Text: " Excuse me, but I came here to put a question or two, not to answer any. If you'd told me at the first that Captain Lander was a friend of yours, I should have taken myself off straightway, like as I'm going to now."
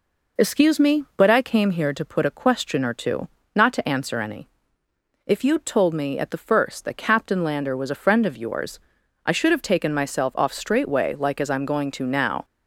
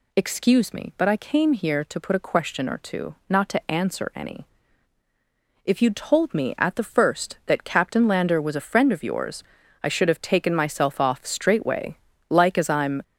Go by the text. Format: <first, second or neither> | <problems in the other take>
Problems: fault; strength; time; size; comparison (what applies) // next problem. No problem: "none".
first | stops before "going to now"; at 13.0 s